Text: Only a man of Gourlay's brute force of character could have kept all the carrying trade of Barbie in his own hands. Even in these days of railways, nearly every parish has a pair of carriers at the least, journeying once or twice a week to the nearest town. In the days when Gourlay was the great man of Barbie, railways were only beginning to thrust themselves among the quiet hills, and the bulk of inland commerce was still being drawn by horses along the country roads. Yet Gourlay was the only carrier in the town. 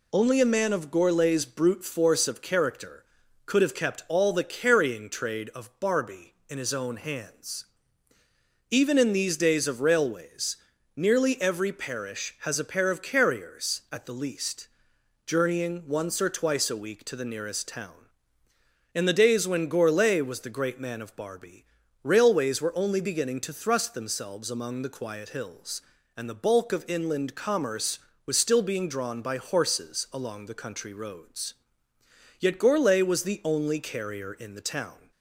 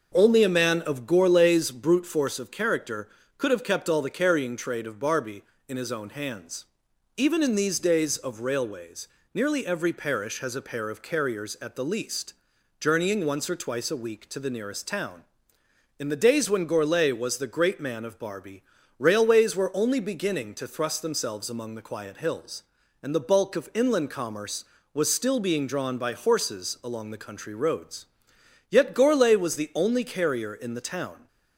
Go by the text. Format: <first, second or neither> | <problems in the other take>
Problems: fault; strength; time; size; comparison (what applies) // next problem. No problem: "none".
neither | none